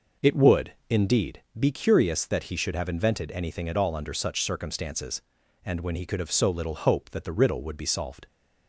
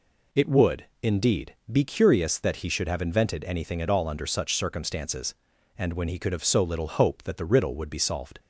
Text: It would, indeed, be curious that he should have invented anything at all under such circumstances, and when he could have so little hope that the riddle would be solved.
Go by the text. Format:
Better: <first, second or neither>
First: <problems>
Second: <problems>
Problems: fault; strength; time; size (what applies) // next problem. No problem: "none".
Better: second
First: starts louder than the rest; noticeable; until 1.2 s; 5.5 dB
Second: none